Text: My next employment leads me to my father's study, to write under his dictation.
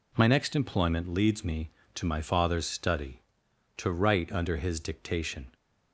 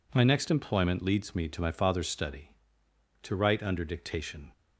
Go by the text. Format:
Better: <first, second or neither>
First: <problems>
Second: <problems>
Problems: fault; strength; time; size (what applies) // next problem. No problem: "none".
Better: first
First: none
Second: skips "his"; at 3.8 s